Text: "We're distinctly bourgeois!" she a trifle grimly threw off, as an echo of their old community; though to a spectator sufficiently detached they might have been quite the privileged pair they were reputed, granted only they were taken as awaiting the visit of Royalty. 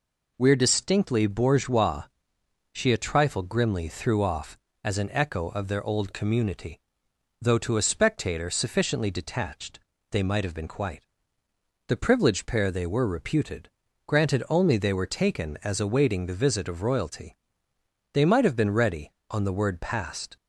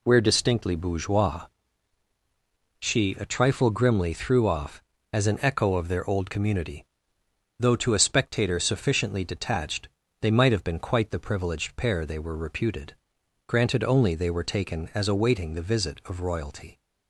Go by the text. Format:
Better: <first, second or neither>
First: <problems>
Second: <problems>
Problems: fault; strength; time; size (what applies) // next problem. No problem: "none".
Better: second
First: pauses between "detached" and "they"; slight; at 9.7 s; 0.32 s long // pauses between "quite" and "the"; noticeable; at 11.0 s; 0.80 s long // goes on to say "They might have been ready on the word passed"; strong; from 18.1 s on; 2.2 s long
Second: pauses between "detached" and "they"; slight; at 9.8 s; 0.34 s long